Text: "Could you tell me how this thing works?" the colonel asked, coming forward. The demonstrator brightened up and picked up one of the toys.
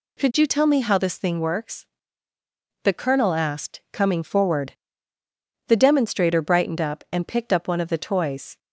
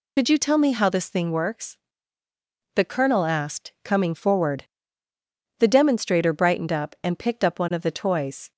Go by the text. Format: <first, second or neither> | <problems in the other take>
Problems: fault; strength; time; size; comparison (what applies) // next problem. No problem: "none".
first | loses the start of "Could"; at 0.1 s; 55 ms